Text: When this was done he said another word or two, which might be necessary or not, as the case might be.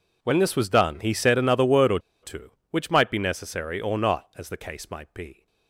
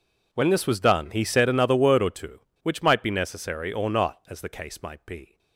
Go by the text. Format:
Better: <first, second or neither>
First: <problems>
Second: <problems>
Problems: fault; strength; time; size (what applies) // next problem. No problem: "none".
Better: second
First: pauses between "or" and "two"; slight; at 1.9 s; 0.24 s long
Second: none